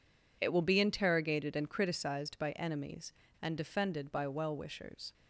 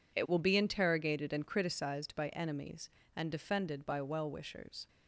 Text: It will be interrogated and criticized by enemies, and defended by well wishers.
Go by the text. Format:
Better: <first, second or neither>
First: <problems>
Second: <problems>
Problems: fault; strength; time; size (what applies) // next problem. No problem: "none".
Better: neither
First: none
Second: none